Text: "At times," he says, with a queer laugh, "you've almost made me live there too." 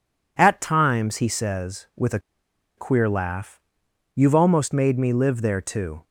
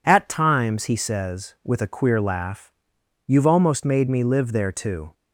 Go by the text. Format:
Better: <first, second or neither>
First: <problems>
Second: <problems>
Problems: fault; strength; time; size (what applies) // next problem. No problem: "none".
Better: second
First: pauses between "a" and "queer"; noticeable; at 2.1 s; 0.58 s long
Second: none